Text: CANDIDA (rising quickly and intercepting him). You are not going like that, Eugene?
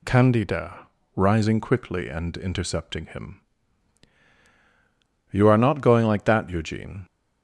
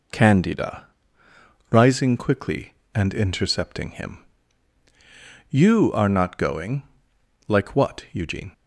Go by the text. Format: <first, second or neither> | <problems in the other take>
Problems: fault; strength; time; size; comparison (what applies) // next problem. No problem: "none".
first | pauses between "going" and "like"; noticeable; at 6.8 s; 0.64 s long // says "what" for "that"; at 7.7 s